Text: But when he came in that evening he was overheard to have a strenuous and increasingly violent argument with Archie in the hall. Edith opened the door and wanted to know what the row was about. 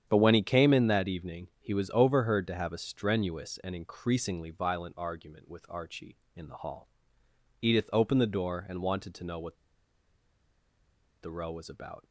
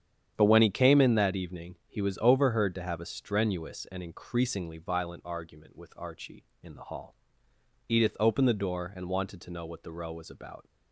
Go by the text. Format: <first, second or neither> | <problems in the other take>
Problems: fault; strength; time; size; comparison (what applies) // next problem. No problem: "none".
second | starts louder than the rest; strong; until 1.0 s; 9 dB; strong in the second // pauses between "what" and "the"; strong; at 9.5 s; 1.6 s long